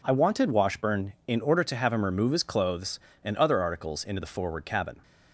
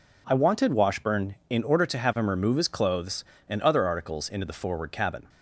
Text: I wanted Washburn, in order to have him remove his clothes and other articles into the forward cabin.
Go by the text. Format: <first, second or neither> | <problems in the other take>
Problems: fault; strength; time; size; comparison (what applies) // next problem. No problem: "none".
neither | none